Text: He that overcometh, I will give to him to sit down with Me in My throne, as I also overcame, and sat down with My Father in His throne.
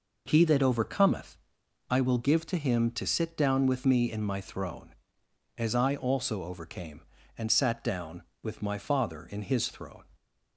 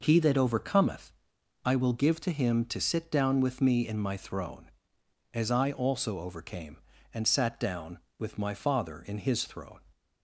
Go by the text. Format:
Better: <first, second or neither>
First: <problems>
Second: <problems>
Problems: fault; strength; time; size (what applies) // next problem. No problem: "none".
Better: neither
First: none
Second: none